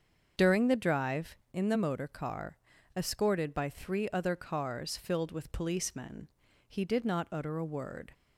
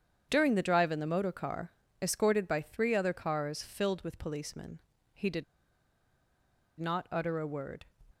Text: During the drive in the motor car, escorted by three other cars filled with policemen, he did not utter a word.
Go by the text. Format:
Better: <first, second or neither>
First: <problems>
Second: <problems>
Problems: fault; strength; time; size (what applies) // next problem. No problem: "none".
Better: first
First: starts louder than the rest; until 1.5 s; 7 dB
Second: starts louder than the rest; strong; until 1.3 s; 8 dB // pauses between "did" and "not"; strong; at 5.4 s; 1.3 s long